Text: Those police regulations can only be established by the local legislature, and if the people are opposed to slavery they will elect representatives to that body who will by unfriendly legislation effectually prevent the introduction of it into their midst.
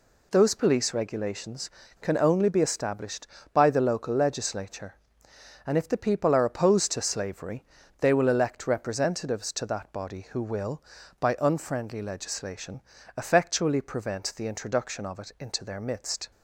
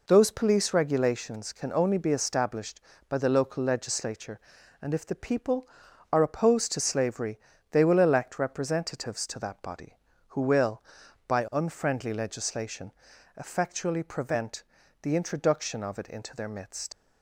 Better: first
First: pauses between "slavery" and "they"; slight; at 7.6 s; 0.34 s long // pauses between "legislation" and "effectually"; slight; at 12.8 s; 0.36 s long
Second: pauses between "slavery" and "they"; slight; at 7.3 s; 0.32 s long // pauses between "legislation" and "effectually"; at 12.9 s; 0.44 s long // pauses between "prevent" and "the"; at 14.6 s; 0.38 s long // leaves "midst" unfinished; at 16.9 s; 90 ms

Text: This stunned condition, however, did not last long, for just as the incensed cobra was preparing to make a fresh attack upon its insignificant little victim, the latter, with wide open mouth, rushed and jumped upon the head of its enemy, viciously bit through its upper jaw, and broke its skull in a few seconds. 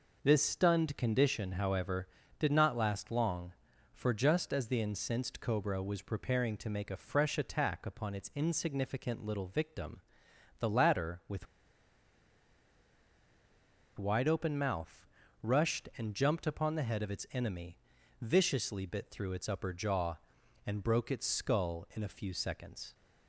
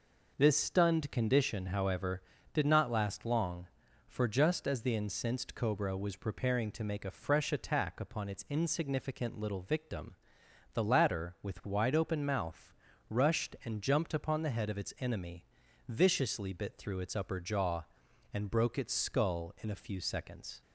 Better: second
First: pauses between "with" and "wide"; strong; at 11.4 s; 2.5 s long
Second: none

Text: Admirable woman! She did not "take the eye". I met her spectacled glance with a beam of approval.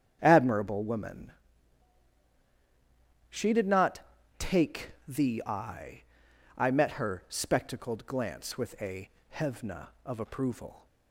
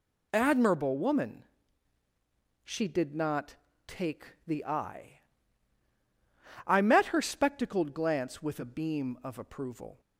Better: second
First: starts louder than the rest; strong; until 1.2 s; 8.5 dB // pauses between "not" and "take"; at 3.9 s; 0.40 s long // says "hevna" for "beam"; at 9.3 s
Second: pauses between "not" and "take"; slight; at 3.5 s; 0.32 s long

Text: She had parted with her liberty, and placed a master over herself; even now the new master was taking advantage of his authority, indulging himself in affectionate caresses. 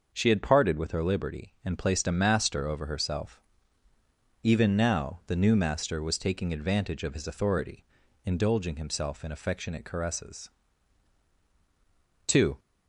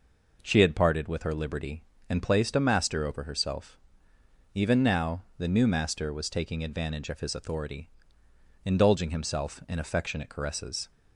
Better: second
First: starts louder than the rest; until 1.1 s; 6.5 dB // goes on to say "Two"; slight; from 12.2 s on; 0.32 s long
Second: none

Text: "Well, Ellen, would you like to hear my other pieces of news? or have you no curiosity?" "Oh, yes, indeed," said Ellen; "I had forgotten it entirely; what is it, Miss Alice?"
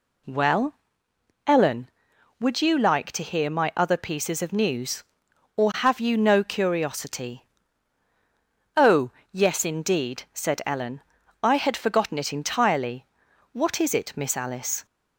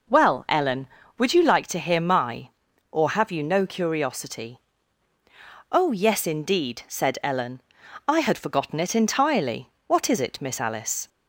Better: first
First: none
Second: skips "other pieces of news"; at 2.7 s

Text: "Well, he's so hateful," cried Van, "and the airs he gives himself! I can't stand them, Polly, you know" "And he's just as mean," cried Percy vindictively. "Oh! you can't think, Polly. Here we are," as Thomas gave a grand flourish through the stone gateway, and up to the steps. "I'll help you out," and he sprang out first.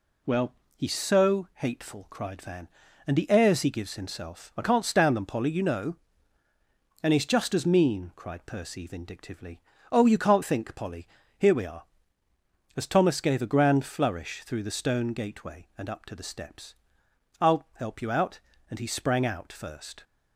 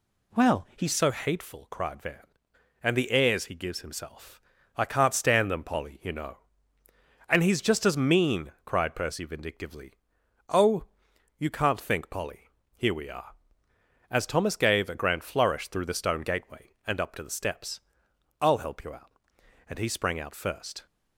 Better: first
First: none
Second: changes voice at "so"; from 0.9 s on; 19.9 s long

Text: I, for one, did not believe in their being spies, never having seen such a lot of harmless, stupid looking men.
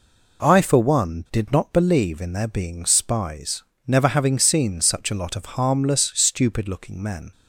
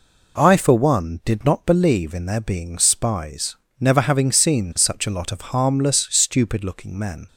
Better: neither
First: none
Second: none

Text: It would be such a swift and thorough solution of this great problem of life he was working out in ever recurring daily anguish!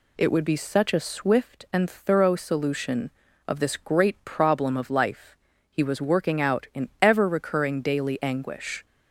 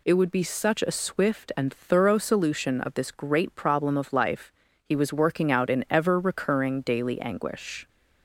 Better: neither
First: pauses between "life" and "he"; slight; at 5.3 s; 0.34 s long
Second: pauses between "life" and "he"; slight; at 4.5 s; 0.30 s long

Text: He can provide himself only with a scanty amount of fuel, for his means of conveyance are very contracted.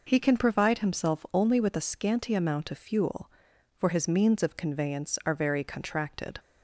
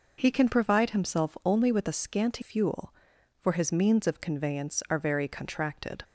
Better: first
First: none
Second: skips "amount of"; at 2.4 s

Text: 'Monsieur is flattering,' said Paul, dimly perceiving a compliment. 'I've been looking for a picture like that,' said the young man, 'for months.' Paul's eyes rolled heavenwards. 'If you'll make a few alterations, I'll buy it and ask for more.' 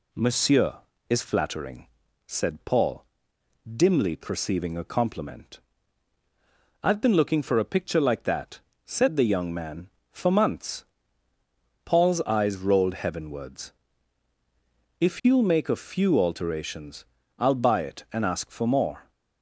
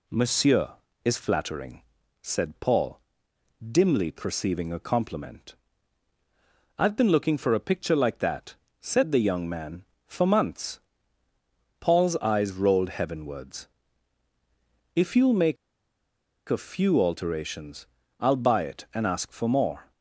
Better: first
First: none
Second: pauses between "make" and "a"; noticeable; at 15.5 s; 0.93 s long

